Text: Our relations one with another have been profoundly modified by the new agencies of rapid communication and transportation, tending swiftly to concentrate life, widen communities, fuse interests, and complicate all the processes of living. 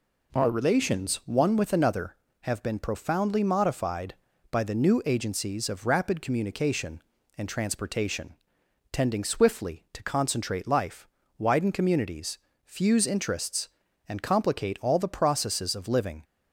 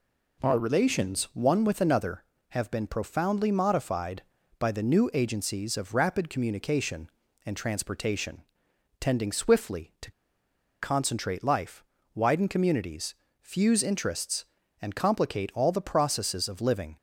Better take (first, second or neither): first